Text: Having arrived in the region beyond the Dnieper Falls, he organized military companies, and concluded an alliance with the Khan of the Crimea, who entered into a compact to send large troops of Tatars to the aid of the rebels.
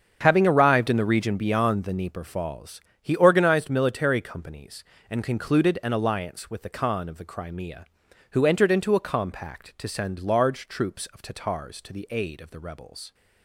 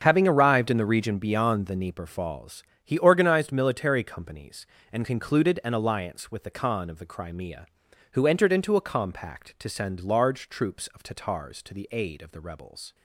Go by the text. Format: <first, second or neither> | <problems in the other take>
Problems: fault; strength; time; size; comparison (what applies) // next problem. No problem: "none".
neither | starts louder than the rest; the same in both